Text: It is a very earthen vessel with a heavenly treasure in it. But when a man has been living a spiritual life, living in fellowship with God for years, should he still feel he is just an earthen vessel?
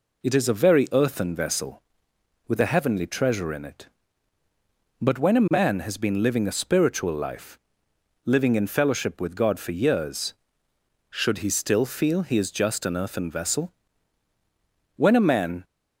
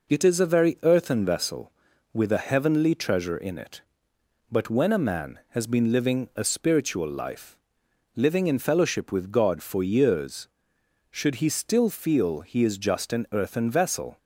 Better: second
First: goes on to say "When a man"; noticeable; from 14.9 s on; 0.68 s long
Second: none

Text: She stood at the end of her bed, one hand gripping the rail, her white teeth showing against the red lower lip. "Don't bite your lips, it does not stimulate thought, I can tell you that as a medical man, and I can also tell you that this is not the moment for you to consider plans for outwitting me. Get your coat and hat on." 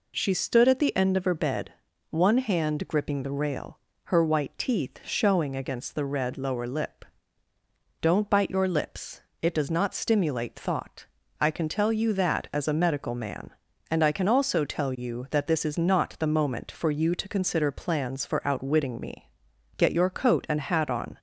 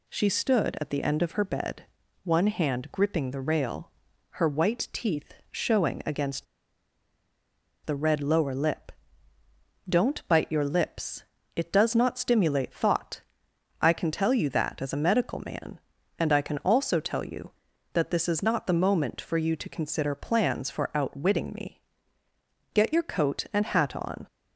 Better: first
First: none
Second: pauses between "teeth" and "showing"; slight; at 5.3 s; 0.18 s long // pauses between "against" and "the"; strong; at 6.4 s; 1.4 s long

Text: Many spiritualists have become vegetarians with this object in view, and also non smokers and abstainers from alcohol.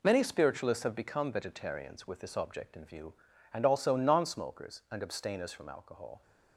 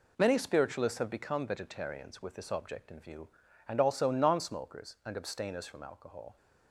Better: neither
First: none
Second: none

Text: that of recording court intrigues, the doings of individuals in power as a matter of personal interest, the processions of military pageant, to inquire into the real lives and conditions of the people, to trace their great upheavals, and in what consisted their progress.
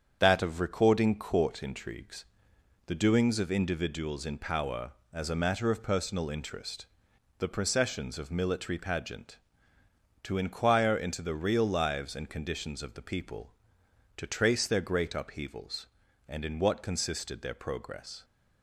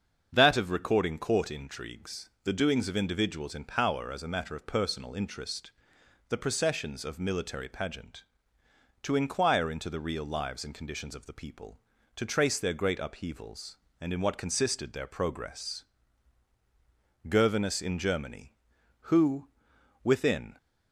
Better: first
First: starts louder than the rest; strong; until 1.2 s; 7.5 dB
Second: starts louder than the rest; until 1.3 s; 7 dB // goes on to say "Gervinus in Germany who within"; strong; from 17.2 s on; 3.3 s long

